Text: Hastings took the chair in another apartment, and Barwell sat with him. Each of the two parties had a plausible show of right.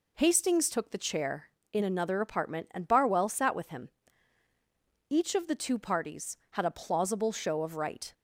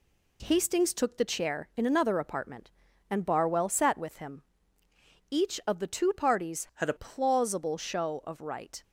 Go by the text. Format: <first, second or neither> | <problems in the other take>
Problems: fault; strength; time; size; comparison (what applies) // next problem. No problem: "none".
first | changes voice from "had" to "a"; from 6.7 to 6.9 s; 0.2 s long